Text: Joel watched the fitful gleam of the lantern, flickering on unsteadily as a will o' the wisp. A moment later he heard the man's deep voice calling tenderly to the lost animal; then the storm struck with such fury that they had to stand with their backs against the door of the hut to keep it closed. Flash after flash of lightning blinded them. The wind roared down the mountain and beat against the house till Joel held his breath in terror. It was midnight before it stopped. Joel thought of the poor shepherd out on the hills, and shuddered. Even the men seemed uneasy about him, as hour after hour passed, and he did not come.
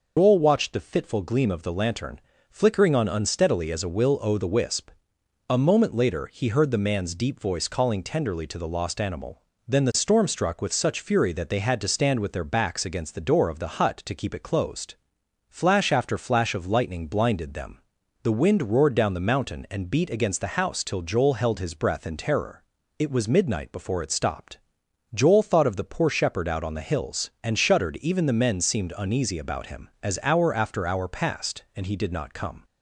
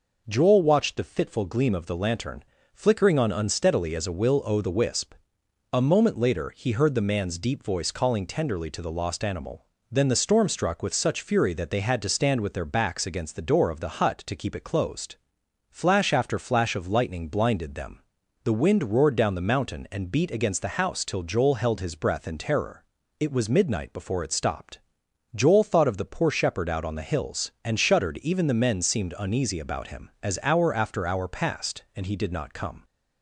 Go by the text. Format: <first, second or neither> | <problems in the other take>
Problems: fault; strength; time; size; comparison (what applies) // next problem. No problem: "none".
second | loses the start of "Joel"; at 0.1 s; 140 ms